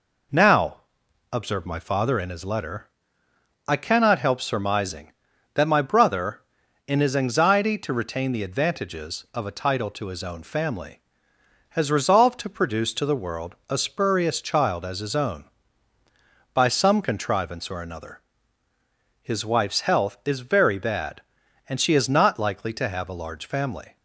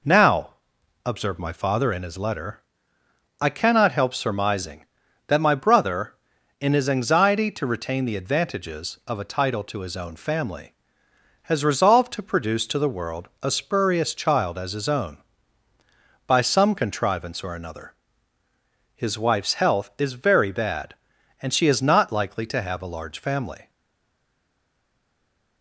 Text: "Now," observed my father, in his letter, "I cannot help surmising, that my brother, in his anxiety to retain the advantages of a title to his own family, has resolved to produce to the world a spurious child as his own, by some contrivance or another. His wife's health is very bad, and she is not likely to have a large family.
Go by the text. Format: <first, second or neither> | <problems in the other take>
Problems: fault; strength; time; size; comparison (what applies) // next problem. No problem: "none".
first | stays silent after the last word; noticeable; from 23.6 s on; 2.0 s long